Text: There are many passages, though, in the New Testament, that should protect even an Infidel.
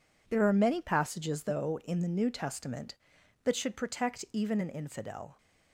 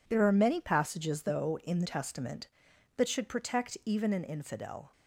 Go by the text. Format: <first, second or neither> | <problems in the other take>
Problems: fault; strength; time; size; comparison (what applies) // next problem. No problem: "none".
first | skips "New"; at 1.8 s